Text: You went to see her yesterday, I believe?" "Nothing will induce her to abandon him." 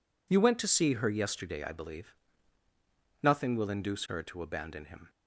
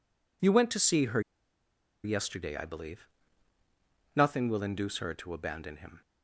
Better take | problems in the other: first | pauses between "her" and "yesterday"; noticeable; at 1.1 s; 0.84 s long

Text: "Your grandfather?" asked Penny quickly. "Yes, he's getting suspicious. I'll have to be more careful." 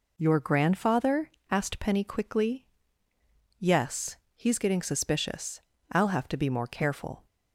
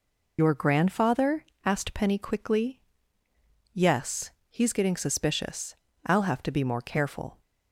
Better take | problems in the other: first | loses the start of "Your"; at 0.3 s; 60 ms

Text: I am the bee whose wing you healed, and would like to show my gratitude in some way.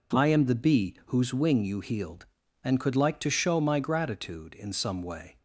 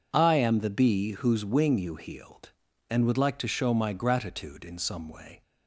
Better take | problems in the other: second | says "could" for "would"; at 2.7 s

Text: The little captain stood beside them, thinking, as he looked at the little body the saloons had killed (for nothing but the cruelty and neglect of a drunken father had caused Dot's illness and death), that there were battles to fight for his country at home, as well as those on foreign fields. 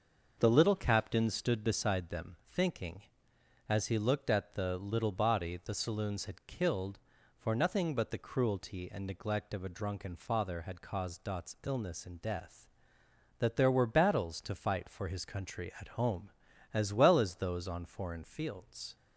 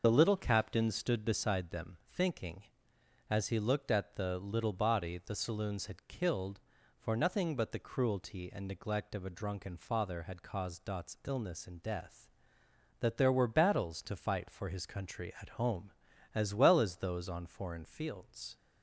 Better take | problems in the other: first | loses the start of "The"; at 0.0 s; 40 ms // starts louder than the rest; noticeable; until 1.0 s; 6 dB; also in the first

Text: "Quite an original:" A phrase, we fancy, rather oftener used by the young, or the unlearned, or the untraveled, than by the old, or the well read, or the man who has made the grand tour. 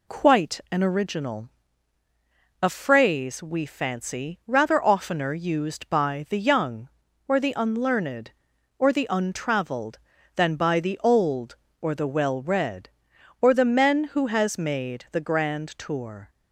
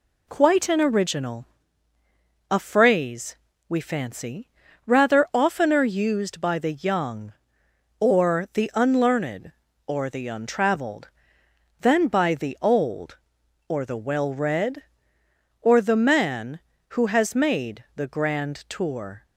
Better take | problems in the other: second | says "men" for "man"; at 13.6 s

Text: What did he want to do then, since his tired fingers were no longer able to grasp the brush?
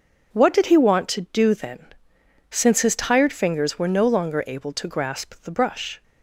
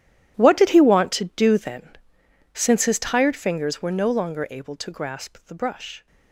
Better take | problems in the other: first | gets quieter; strong; throughout; 18.5 dB

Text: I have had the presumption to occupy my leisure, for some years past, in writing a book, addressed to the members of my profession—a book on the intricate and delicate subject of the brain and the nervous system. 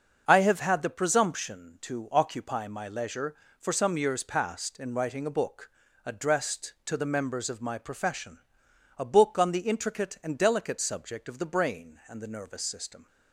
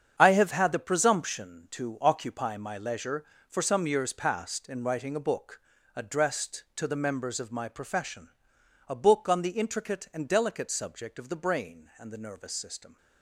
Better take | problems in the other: first | gets quieter; strong; throughout; 10.5 dB // starts louder than the rest; strong; until 1.1 s; 8 dB; also in the first

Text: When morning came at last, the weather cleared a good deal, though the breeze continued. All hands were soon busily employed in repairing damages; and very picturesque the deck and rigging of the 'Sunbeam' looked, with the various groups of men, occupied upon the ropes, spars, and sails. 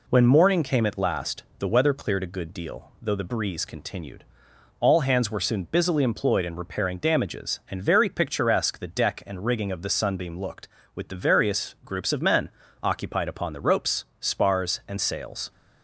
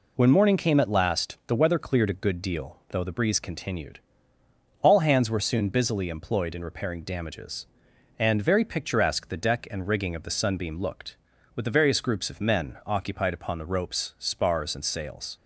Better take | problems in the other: neither | none

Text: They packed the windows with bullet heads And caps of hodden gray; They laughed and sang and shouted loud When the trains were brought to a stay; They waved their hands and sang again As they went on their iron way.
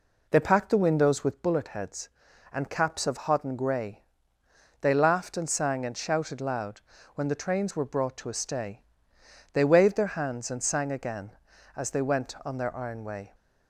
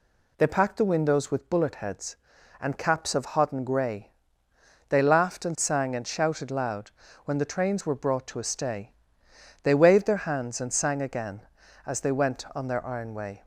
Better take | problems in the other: second | starts louder than the rest; until 1.5 s; 3.5 dB // pauses between "loud" and "When"; slight; at 6.8 s; 0.34 s long; slight in the second

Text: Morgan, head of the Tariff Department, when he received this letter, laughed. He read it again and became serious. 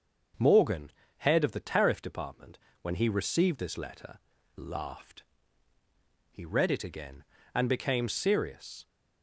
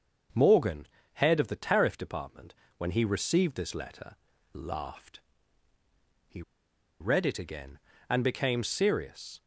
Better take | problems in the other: first | starts louder than the rest; until 1.6 s; 6.5 dB; also in the first // pauses between "He" and "read"; noticeable; at 6.4 s; 0.59 s long

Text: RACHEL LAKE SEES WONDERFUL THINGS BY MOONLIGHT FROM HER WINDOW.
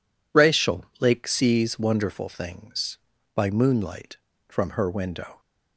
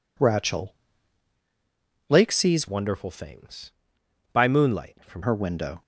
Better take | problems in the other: first | pauses between "RACHEL" and "LAKE"; strong; at 0.7 s; 1.3 s long; slight in the first // changes voice from "WONDERFUL" to "FROM"; from 2.6 to 5.2 s; 2.6 s long

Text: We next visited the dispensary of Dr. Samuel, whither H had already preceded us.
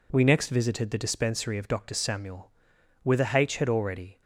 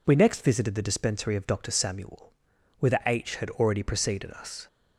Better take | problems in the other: second | stops before "preceded us"; at 4.2 s

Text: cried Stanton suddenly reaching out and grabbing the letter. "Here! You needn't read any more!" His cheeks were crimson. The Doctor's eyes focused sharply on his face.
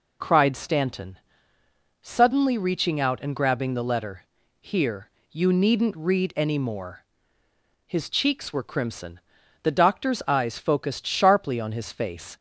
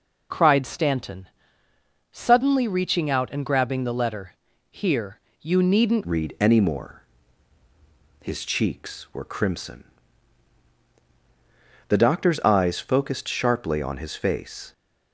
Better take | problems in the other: first | pauses between "Stanton" and "suddenly"; noticeable; at 1.2 s; 0.86 s long; noticeable in the first // changes voice at "read"; from 6.0 s on; 8.7 s long

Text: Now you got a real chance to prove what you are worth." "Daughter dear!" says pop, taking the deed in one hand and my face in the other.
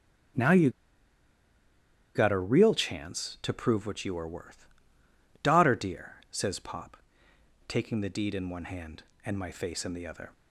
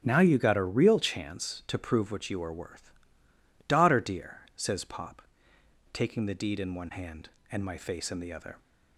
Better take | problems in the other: second | starts louder than the rest; strong; until 2.8 s; 10.5 dB; strong in the second // pauses between "you" and "got"; strong; at 0.6 s; 1.4 s long

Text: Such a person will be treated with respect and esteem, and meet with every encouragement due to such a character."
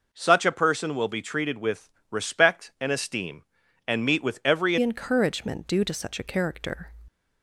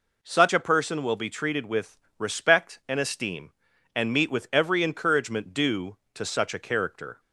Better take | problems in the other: second | pauses between "with" and "respect"; slight; at 1.8 s; 0.20 s long; slight in the second // changes voice at "encouragement"; from 4.8 s on; 2.0 s long

